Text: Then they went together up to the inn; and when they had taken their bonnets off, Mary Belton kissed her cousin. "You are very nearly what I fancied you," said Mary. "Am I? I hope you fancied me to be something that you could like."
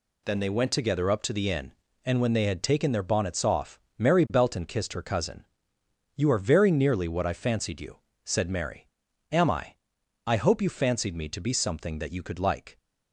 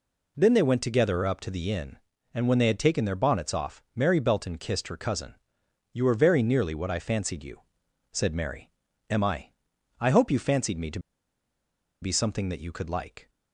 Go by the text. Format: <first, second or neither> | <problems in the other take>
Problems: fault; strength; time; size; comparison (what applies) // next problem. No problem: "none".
first | pauses between "to" and "be"; at 10.9 s; 1.0 s long